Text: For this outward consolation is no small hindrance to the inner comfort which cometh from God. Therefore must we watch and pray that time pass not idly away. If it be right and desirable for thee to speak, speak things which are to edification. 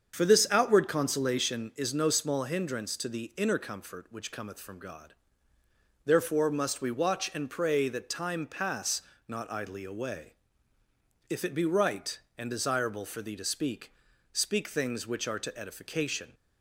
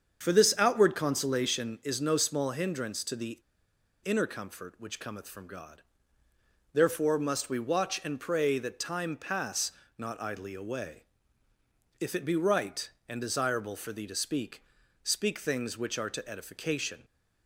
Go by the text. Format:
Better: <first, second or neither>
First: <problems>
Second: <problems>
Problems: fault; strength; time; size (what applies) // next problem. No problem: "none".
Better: first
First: starts louder than the rest; strong; until 1.1 s; 7.5 dB // pauses between "pass" and "not"; slight; at 9.0 s; 0.26 s long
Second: starts louder than the rest; strong; until 1.2 s; 7.5 dB // pauses between "the" and "inner"; noticeable; at 3.3 s; 0.64 s long // pauses between "pass" and "not"; slight; at 9.7 s; 0.26 s long